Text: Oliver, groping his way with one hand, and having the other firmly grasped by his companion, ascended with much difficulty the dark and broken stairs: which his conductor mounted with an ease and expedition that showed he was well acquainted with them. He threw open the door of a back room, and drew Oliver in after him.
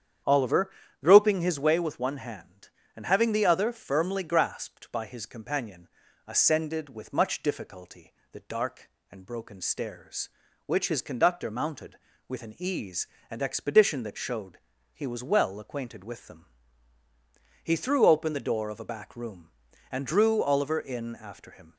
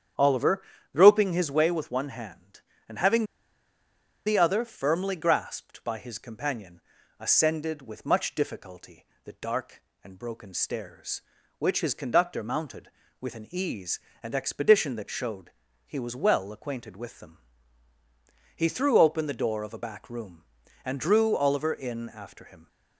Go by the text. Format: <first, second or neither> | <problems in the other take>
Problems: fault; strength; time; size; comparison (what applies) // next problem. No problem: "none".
first | starts louder than the rest; strong; until 1.5 s; 8.5 dB; strong in the first // pauses between "having" and "the"; at 3.2 s; 1.0 s long // pauses between "difficulty" and "the"; slight; at 9.0 s; 0.20 s long; slight in the first // pauses between "showed" and "he"; slight; at 15.5 s; 0.34 s long; slight in the first